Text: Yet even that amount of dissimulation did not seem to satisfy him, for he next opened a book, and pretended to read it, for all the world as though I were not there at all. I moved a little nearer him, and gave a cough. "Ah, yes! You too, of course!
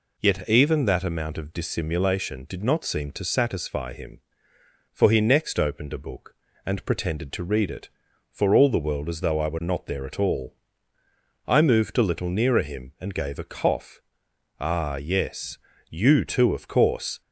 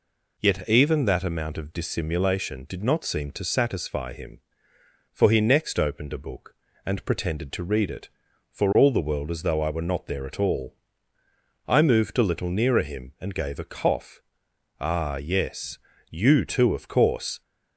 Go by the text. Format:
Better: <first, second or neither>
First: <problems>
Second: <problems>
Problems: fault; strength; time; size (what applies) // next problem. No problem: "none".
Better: neither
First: none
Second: none